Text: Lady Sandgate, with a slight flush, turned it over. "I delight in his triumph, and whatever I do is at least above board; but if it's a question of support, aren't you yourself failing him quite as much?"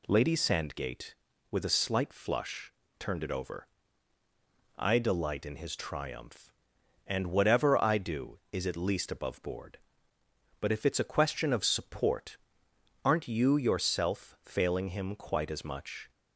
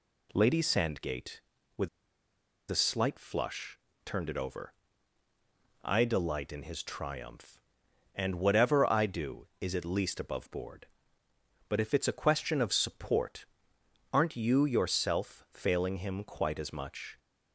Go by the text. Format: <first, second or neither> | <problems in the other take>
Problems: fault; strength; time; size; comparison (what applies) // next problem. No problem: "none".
first | pauses between "with" and "a"; noticeable; at 1.8 s; 0.81 s long